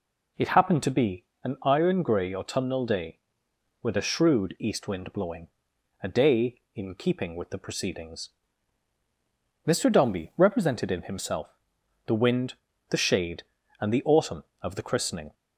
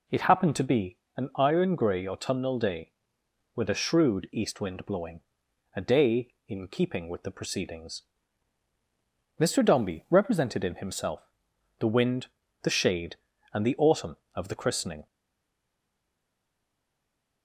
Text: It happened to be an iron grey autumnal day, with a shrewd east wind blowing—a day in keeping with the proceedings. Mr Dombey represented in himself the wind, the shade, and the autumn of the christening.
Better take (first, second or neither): first